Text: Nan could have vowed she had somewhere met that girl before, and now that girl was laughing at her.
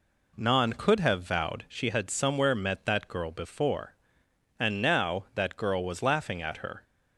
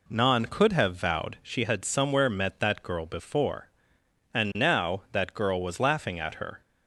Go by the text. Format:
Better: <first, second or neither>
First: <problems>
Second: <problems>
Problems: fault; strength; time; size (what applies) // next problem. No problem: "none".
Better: neither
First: none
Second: none